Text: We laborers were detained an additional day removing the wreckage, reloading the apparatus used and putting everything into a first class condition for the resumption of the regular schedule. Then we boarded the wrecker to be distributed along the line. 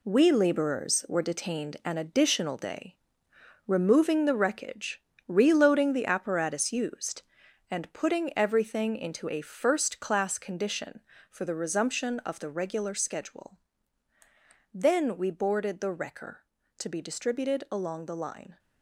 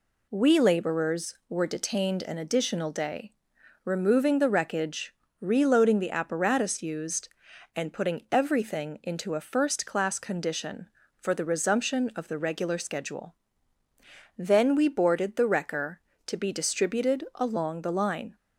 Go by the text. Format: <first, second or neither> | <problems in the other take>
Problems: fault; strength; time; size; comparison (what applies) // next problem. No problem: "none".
second | gets quieter; strong; throughout; 8.5 dB // pauses between "day" and "removing"; noticeable; at 2.9 s; 0.70 s long; noticeable in the second